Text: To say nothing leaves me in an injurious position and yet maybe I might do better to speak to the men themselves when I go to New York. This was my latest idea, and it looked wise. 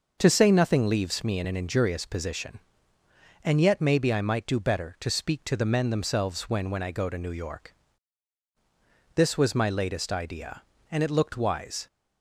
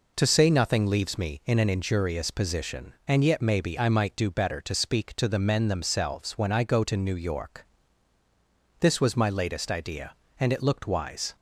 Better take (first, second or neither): second